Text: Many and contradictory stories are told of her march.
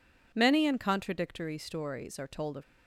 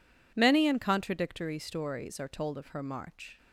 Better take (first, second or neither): second